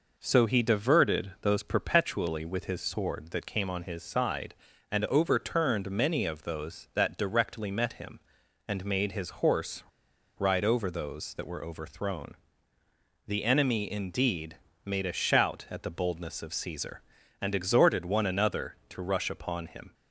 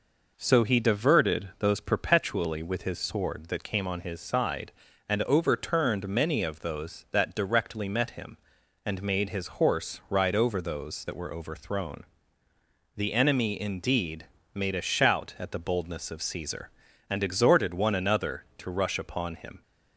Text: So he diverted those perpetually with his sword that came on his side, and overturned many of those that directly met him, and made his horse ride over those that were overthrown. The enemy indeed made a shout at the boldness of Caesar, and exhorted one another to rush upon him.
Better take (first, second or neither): second